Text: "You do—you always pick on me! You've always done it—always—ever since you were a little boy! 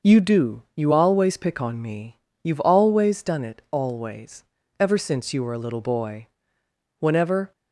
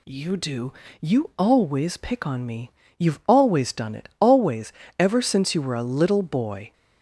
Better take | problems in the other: second | starts louder than the rest; noticeable; until 1.1 s; 6 dB // goes on to say "Whenever"; from 6.9 s on; 0.52 s long

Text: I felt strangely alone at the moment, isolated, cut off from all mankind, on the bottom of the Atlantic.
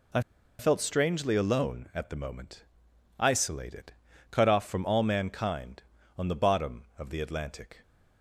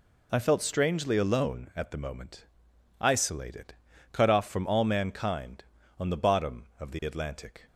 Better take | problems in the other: second | pauses between "I" and "felt"; at 0.1 s; 0.39 s long

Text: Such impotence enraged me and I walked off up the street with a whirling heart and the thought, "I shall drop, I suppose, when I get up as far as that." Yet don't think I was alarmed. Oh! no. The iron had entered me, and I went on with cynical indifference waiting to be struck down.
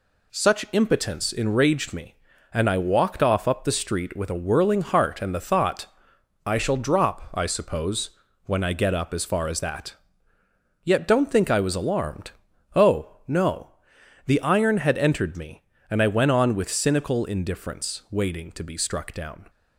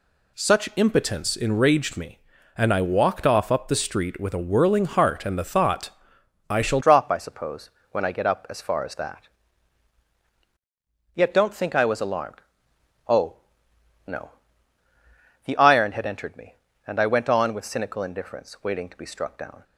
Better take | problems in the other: first | changes voice at "drop"; from 6.8 s on; 12.8 s long

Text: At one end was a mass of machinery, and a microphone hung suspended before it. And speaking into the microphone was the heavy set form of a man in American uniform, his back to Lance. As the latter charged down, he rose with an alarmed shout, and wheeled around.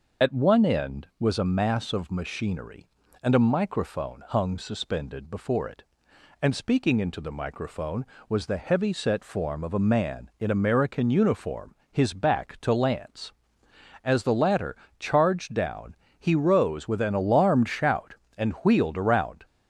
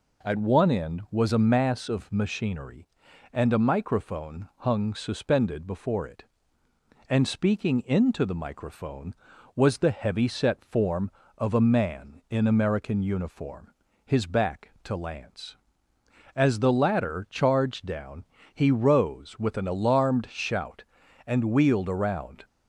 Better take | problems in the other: second | loses the start of "At"; at 0.2 s; 30 ms // pauses between "latter" and "charged"; slight; at 14.7 s; 0.24 s long

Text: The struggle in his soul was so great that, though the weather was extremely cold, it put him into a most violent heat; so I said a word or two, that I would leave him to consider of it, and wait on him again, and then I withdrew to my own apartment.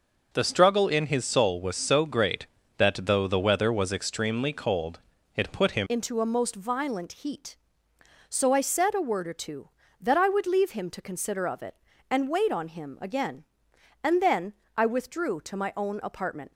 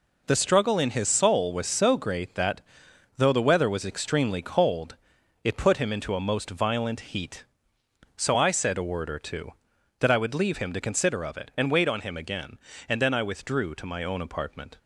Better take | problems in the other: second | changes voice at "into"; from 5.8 s on; 10.7 s long // pauses between "then" and "I"; slight; at 14.5 s; 0.24 s long

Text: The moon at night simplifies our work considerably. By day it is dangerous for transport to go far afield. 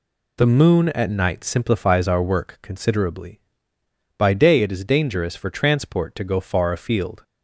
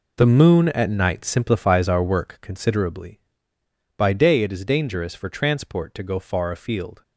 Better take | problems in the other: first | gets quieter; strong; throughout; 12.5 dB

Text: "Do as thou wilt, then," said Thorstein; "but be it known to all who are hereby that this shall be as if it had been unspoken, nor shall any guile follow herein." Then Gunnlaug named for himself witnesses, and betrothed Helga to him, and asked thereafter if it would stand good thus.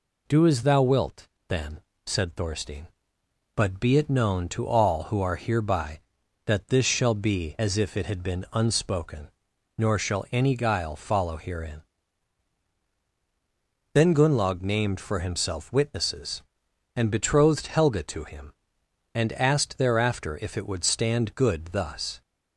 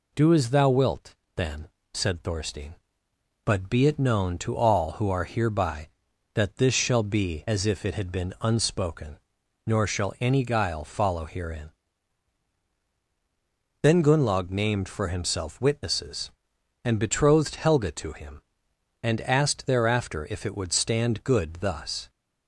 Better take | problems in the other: neither | none

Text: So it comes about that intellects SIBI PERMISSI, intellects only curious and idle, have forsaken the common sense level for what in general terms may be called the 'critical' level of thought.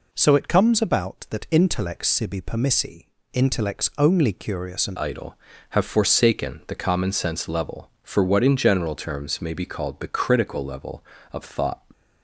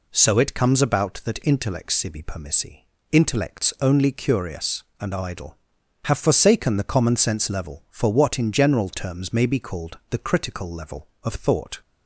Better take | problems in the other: second | changes voice at "idle"; from 4.9 s on; 6.9 s long

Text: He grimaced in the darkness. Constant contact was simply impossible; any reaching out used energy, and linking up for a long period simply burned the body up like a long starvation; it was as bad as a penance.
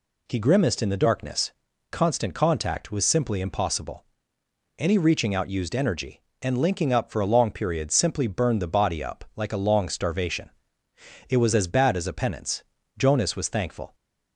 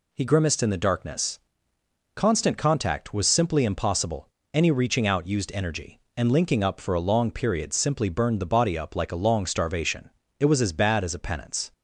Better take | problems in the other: second | goes on to say "Jonas was thankful"; noticeable; from 12.9 s on; 0.98 s long

